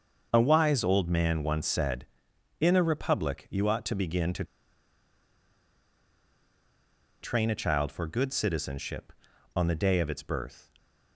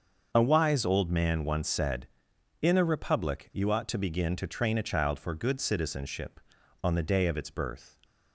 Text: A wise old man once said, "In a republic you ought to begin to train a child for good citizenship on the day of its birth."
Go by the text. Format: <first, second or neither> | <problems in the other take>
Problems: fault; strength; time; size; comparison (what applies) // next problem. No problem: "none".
second | starts louder than the rest; until 1.3 s; 6.5 dB; also in the second // pauses between "to" and "train"; strong; at 4.4 s; 2.7 s long